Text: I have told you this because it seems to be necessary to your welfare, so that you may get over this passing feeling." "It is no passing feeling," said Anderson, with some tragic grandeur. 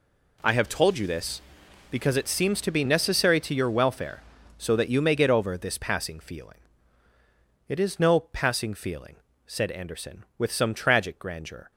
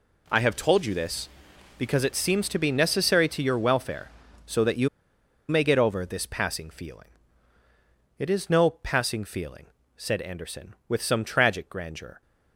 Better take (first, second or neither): first